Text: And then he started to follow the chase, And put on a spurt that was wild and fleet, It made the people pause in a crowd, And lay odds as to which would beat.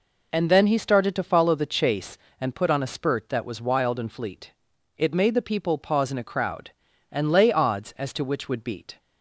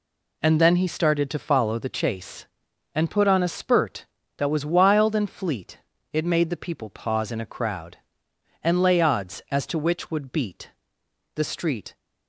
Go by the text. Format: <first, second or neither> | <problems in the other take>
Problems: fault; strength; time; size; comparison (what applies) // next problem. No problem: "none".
first | goes on to say "The street"; noticeable; from 11.3 s on; 0.62 s long